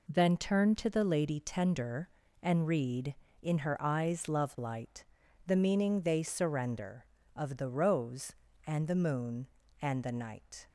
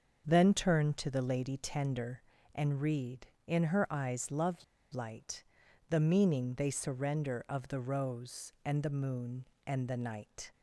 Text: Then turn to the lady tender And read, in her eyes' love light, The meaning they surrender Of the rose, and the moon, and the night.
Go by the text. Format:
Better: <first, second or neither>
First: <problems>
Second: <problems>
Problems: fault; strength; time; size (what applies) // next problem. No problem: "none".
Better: first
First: none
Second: starts louder than the rest; until 1.2 s; 6.5 dB // pauses between "love" and "light"; slight; at 4.6 s; 0.29 s long